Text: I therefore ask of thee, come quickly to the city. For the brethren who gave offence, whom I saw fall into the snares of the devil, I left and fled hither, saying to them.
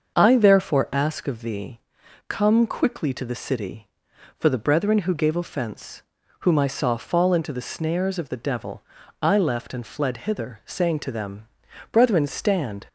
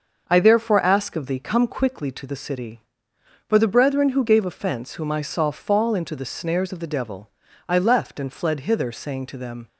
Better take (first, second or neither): second